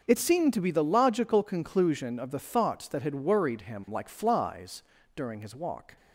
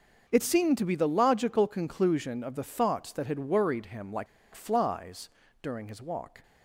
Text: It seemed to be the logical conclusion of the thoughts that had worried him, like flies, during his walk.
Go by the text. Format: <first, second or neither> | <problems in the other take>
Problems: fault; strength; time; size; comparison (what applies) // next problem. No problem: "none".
first | starts louder than the rest; until 1.3 s; 6.5 dB; also in the first // pauses between "like" and "flies"; slight; at 4.2 s; 0.28 s long